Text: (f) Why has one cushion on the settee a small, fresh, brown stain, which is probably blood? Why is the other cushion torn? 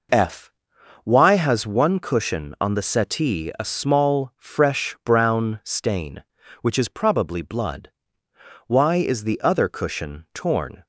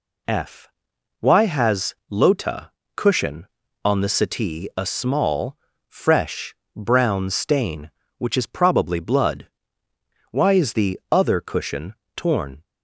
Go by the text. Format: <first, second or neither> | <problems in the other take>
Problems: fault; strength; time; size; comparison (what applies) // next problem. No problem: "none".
first | says "lota" for "one"; at 2.0 s // pauses between "cushion" and "torn"; slight; at 11.9 s; 0.22 s long